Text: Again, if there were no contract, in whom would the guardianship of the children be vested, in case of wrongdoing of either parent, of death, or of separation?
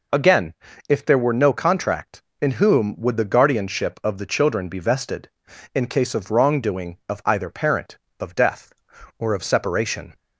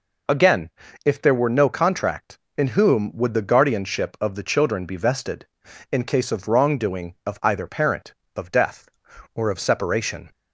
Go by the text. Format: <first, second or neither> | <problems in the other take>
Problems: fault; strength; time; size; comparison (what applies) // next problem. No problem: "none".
neither | none